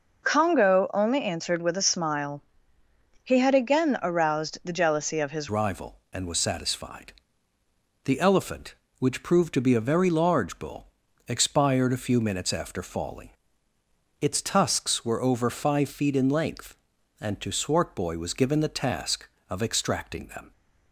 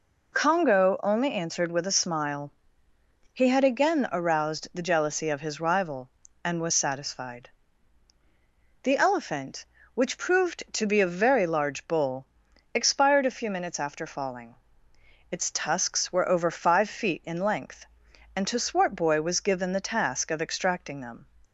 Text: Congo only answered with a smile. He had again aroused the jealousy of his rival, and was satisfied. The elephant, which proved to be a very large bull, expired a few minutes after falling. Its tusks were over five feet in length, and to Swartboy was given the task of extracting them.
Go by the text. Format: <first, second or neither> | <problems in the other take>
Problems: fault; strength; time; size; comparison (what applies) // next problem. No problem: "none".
second | changes voice at "rival"; from 5.4 s on; 15.1 s long